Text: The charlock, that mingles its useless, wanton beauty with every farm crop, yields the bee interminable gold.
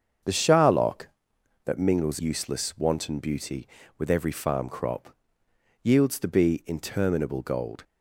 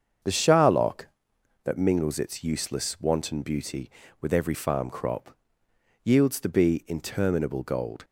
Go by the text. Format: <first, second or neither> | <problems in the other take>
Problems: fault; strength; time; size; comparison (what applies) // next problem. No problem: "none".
second | starts louder than the rest; strong; until 1.8 s; 7 dB; strong in the second // skips "its"; at 2.2 s